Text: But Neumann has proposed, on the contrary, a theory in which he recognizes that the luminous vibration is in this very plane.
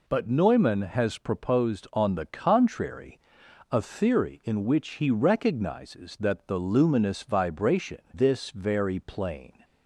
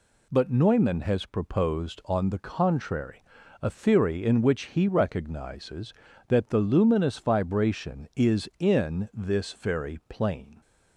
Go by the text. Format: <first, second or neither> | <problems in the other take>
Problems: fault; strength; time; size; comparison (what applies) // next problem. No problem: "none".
second | skips "is in"; at 8.0 s